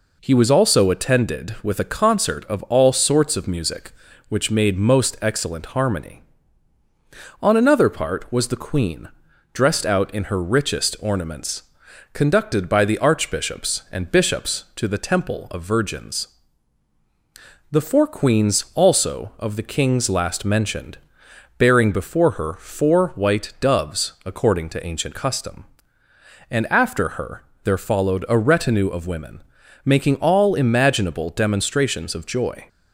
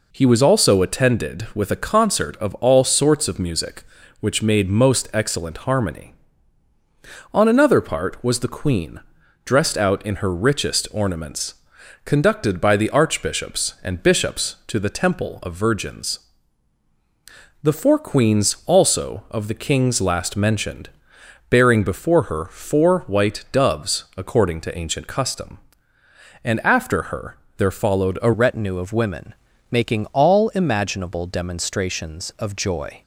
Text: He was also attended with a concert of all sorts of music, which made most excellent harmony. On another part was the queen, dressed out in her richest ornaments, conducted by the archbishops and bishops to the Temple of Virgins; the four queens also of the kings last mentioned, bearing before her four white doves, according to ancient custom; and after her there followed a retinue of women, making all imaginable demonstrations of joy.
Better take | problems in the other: first | pauses between "her" and "there"; slight; at 27.3 s; 0.20 s long; slight in the first // changes voice at "retinue"; from 28.3 s on; 4.7 s long

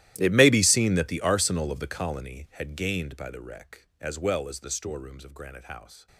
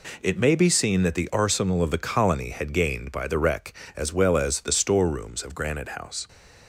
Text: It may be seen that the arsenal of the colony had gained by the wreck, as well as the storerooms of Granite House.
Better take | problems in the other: second | gets quieter; strong; throughout; 21.5 dB

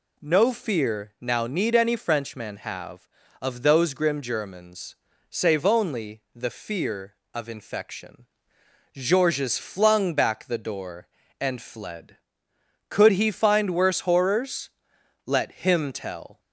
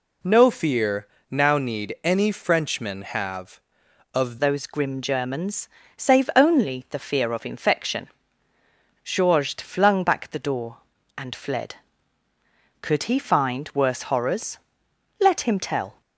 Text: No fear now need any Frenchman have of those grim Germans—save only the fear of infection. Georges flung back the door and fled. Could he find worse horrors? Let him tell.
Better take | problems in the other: first | pauses between "fear" and "now"; slight; at 1.0 s; 0.24 s long // changes voice at "those"; from 4.3 s on; 11.7 s long

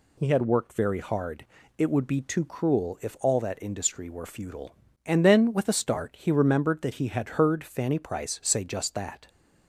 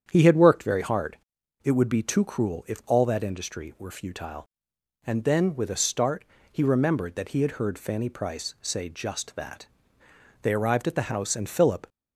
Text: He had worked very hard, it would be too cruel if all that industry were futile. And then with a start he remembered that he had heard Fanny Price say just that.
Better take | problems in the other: first | starts louder than the rest; strong; until 1.1 s; 8.5 dB // pauses between "start" and "he"; slight; at 6.2 s; 0.26 s long // goes on to say "They arrived at the house and Philip"; from 10.4 s on; 1.4 s long

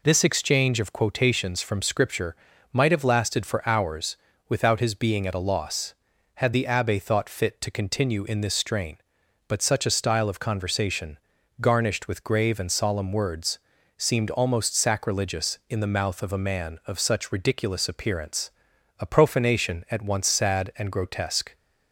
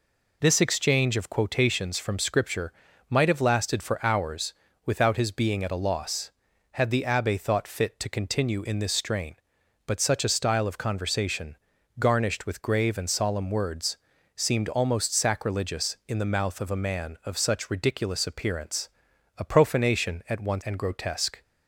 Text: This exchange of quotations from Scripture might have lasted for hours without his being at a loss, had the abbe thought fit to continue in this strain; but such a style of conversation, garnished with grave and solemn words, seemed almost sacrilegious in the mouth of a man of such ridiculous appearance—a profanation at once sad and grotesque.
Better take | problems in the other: first | pauses between "Scripture" and "might"; slight; at 2.7 s; 0.34 s long; slight in the first // pauses between "hours" and "without"; slight; at 4.5 s; 0.30 s long; slight in the first // skips "sad"; at 20.6 s

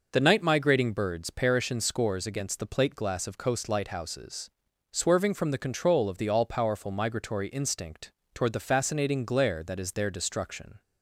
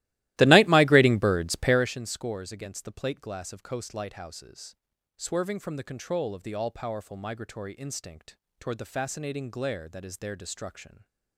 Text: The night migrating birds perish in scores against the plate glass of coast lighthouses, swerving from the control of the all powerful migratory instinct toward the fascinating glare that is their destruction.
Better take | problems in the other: first | starts louder than the rest; strong; until 2.0 s; 17 dB // pauses between "instinct" and "toward"; slight; at 8.3 s; 0.22 s long; slight in the first

